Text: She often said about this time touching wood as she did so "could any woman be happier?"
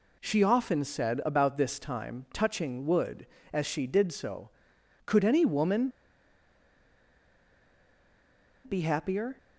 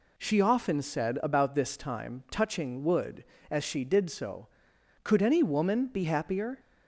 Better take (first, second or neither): second